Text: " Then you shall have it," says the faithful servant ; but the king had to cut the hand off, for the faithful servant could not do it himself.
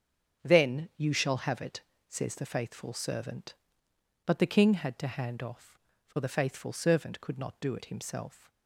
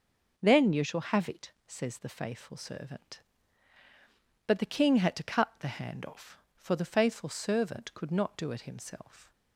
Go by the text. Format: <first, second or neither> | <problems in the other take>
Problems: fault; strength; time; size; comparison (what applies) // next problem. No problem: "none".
second | starts louder than the rest; strong; until 1.4 s; 7.5 dB // skips "cut the"; at 5.0 s